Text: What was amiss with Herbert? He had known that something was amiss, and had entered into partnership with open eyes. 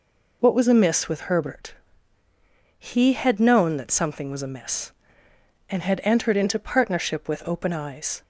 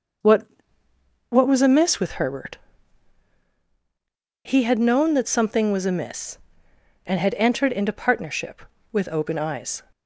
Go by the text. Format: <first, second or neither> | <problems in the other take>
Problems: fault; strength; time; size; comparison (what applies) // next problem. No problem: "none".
first | says "What" twice; at 1.2 s